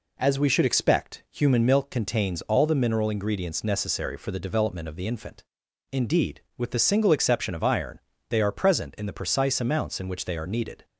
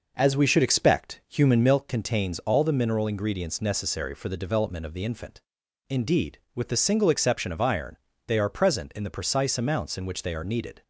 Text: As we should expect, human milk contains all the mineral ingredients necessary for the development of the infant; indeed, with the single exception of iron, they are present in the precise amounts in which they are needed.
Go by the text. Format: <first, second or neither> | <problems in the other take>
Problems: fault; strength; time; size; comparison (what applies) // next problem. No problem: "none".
first | starts louder than the rest; noticeable; until 1.9 s; 5.5 dB